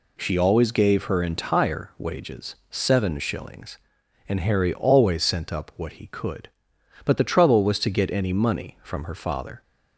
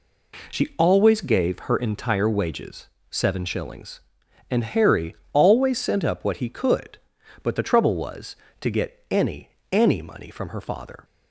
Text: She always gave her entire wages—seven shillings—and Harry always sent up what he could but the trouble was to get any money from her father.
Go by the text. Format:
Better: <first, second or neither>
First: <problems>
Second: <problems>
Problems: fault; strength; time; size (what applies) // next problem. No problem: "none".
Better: first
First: none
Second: pauses between "Harry" and "always"; slight; at 5.1 s; 0.18 s long // says "any" twice; at 9.7 s